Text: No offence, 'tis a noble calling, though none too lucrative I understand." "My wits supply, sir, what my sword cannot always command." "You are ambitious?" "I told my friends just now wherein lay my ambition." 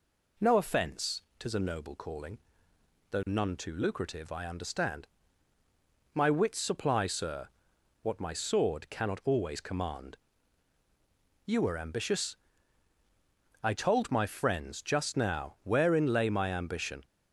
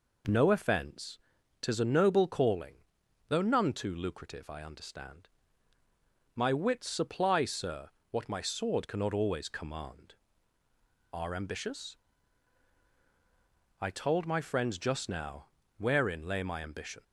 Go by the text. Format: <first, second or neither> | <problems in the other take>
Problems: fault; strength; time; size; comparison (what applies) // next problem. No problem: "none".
first | skips "You"; at 10.6 s // pauses between "now" and "wherein"; slight; at 15.4 s; 0.32 s long